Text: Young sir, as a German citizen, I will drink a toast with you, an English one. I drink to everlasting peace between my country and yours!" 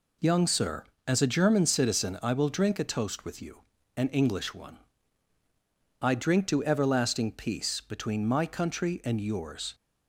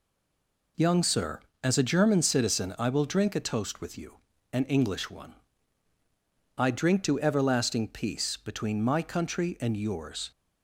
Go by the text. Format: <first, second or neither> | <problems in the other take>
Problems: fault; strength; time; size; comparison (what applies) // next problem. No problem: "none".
first | stays silent before the first word; slight; until 0.7 s; 0.7 s long